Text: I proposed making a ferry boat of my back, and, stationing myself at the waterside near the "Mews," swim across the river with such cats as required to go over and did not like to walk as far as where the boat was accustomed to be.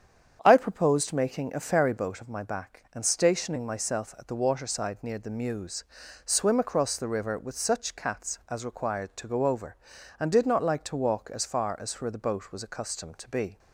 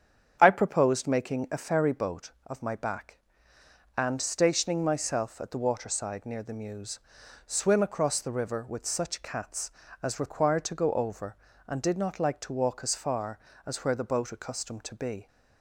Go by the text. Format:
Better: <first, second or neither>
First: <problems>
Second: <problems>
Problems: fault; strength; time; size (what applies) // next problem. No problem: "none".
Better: first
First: starts louder than the rest; strong; until 1.4 s; 8 dB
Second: starts louder than the rest; strong; until 1.4 s; 8 dB // skips "was"; at 14.3 s